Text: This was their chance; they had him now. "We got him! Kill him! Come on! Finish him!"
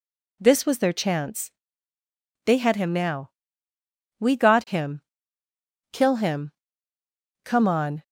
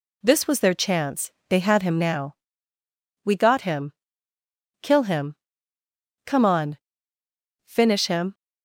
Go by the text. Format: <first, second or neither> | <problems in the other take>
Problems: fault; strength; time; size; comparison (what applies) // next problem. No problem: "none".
second | stops before "Finish him"; at 8.0 s